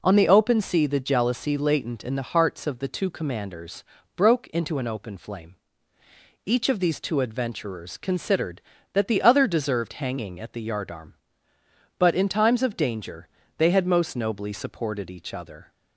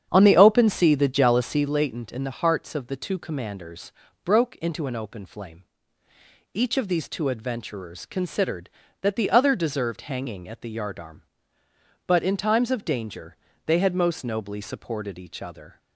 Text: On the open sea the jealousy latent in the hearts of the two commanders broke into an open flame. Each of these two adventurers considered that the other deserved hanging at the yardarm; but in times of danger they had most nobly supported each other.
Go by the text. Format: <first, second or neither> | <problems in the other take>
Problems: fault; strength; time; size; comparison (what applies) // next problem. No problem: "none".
first | starts louder than the rest; strong; until 1.7 s; 8.5 dB // pauses between "commanders" and "broke"; slight; at 3.9 s; 0.32 s long; slight in the first // pauses between "danger" and "they"; slight; at 13.3 s; 0.30 s long; slight in the first